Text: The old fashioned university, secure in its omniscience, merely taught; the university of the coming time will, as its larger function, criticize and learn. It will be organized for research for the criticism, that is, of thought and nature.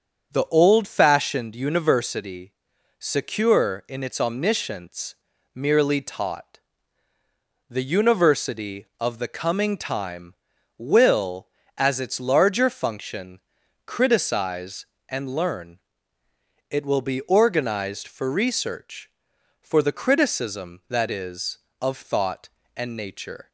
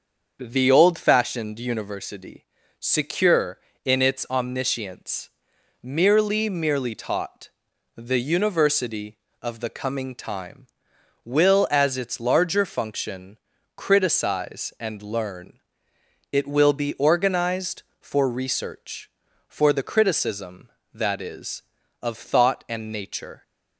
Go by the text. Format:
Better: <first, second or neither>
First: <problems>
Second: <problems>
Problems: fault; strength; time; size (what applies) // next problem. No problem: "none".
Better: first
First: starts louder than the rest; until 1.3 s; 7 dB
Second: starts louder than the rest; until 1.4 s; 6.5 dB // says "merely" twice; at 6.4 s